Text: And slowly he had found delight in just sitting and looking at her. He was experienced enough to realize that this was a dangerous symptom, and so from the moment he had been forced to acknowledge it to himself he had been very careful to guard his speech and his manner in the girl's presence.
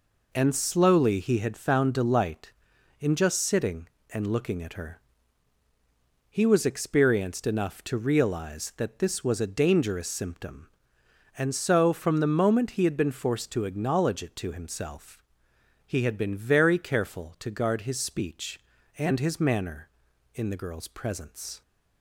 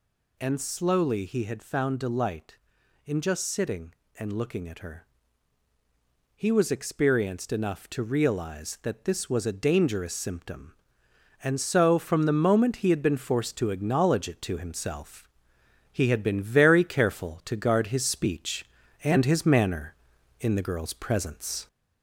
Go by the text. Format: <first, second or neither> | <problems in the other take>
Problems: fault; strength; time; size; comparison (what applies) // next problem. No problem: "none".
first | gets louder; slight; throughout; 2 dB // pauses between "himself" and "he"; noticeable; at 15.2 s; 0.68 s long; noticeable in the first